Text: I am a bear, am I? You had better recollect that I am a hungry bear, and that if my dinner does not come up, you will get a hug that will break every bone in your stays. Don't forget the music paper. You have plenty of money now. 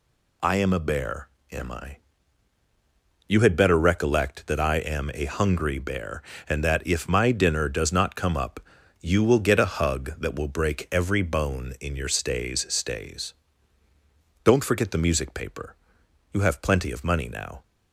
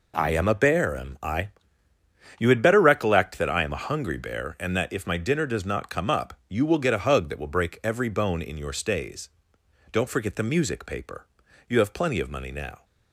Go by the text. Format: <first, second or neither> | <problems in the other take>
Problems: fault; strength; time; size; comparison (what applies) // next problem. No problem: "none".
second | says "stays" twice; at 12.6 s